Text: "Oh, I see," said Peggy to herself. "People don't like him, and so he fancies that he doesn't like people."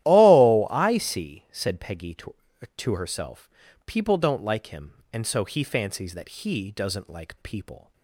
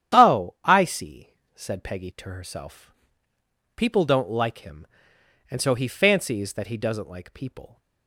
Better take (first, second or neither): second